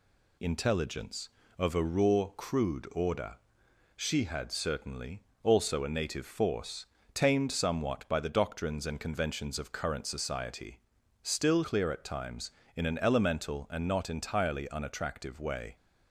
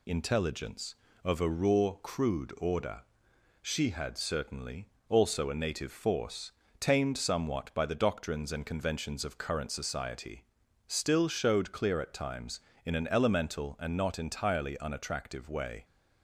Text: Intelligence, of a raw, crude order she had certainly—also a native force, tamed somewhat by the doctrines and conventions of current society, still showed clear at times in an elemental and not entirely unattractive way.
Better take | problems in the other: second | pauses between "order" and "she"; noticeable; at 3.3 s; 0.60 s long; noticeable in the second // skips "showed"; at 11.6 s

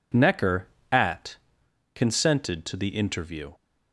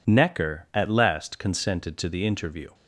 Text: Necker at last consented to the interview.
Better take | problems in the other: second | skips "last"; at 1.6 s

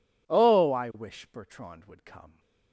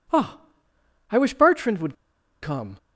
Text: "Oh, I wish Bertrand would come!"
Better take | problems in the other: first | pauses between "would" and "come"; noticeable; at 1.9 s; 0.47 s long

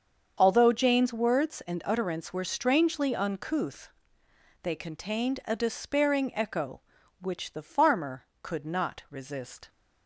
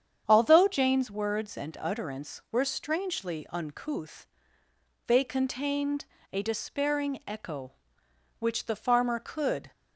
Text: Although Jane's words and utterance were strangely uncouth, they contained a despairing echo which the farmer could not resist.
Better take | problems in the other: first | starts louder than the rest; strong; until 1.2 s; 8 dB; also in the first // pauses between "contained" and "a"; slight; at 6.0 s; 0.28 s long // stops before "not resist"; at 9.7 s

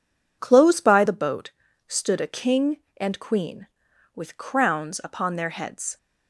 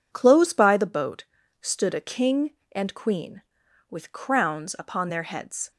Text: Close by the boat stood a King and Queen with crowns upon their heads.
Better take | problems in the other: neither | pauses between "boat" and "stood"; the same in both

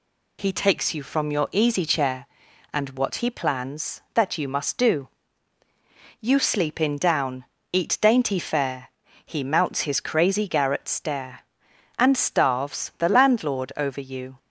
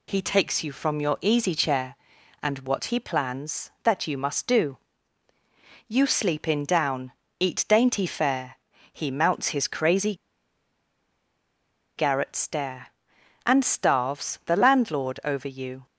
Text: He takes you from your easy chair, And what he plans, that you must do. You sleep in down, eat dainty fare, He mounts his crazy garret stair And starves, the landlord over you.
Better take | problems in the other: first | pauses between "crazy" and "garret"; strong; at 10.1 s; 1.8 s long

